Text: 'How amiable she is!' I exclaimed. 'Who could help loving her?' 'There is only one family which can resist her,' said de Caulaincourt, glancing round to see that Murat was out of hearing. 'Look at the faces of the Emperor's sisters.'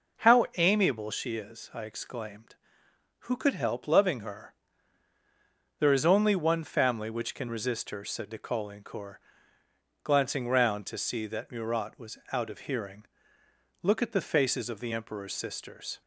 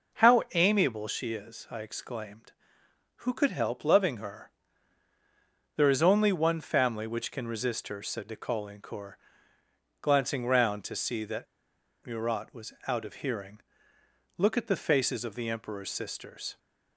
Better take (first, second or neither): first